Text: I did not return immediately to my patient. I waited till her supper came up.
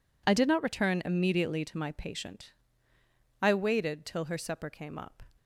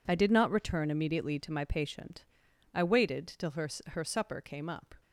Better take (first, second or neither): first